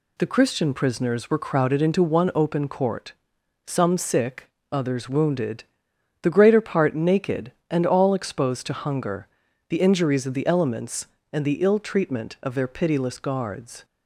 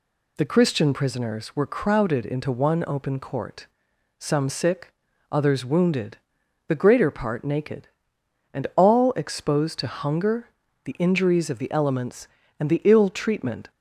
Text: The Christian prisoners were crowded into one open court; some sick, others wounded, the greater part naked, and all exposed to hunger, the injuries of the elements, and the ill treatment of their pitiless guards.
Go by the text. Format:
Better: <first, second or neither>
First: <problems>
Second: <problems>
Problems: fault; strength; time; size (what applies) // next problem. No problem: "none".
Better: first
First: none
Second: stops before "of their pitiless guards"; at 13.7 s